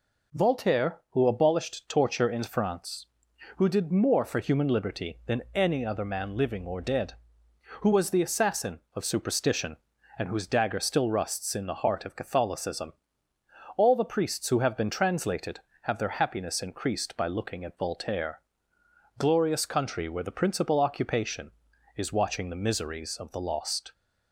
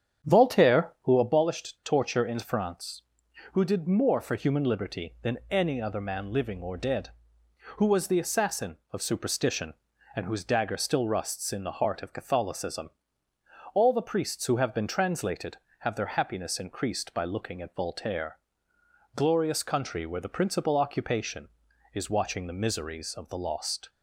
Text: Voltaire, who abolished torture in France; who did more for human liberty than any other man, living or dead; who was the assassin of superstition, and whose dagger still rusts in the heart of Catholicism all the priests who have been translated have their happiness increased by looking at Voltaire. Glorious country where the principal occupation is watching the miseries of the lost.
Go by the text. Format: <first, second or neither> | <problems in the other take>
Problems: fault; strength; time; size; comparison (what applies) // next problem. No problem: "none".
first | starts louder than the rest; strong; until 1.2 s; 8.5 dB // pauses between "Catholicism" and "all"; noticeable; at 12.8 s; 0.82 s long; noticeable in the first